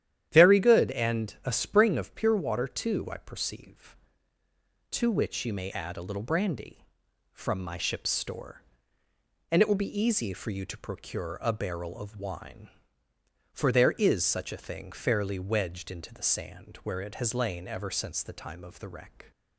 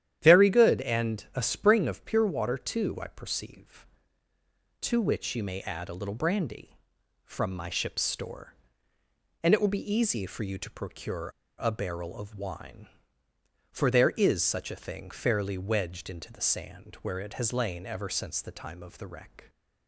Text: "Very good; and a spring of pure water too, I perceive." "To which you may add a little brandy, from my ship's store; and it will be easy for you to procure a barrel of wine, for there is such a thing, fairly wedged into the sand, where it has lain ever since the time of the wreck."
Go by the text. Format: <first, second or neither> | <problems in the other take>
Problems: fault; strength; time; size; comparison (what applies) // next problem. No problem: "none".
first | starts louder than the rest; strong; until 1.2 s; 11 dB; strong in the first // pauses between "procure" and "a"; slight; at 11.2 s; 0.31 s long